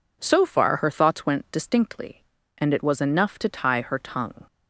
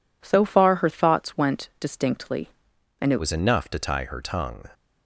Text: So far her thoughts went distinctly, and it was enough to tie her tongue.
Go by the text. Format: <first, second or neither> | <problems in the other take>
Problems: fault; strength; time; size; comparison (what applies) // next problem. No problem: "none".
first | changes voice at "was"; from 3.1 s on; 1.5 s long